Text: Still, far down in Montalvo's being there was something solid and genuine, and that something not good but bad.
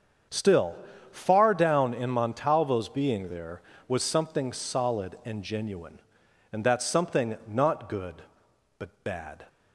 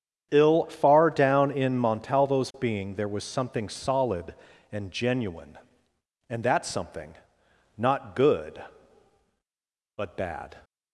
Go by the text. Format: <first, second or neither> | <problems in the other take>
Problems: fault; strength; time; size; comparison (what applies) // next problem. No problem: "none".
first | starts louder than the rest; strong; until 1.3 s; 8.5 dB; strong in the first // says "Ill" for "Still"; at 0.3 s // pauses between "something" and "not"; noticeable; at 7.1 s; 0.62 s long